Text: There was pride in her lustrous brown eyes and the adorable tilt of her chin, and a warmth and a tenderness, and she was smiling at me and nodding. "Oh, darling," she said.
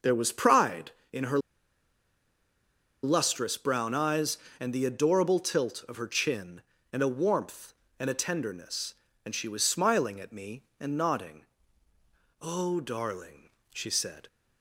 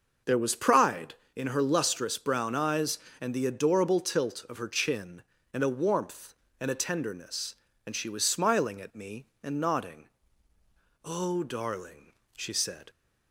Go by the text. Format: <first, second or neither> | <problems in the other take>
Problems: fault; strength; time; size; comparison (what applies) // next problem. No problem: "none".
second | pauses between "her" and "lustrous"; strong; at 1.3 s; 1.6 s long